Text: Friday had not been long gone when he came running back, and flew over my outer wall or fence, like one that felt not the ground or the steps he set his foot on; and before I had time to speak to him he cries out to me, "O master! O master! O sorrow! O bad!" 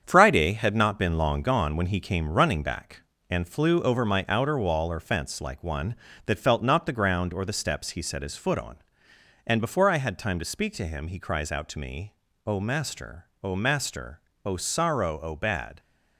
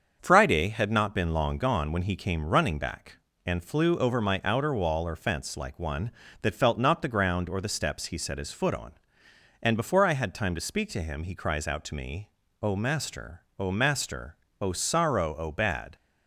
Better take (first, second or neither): second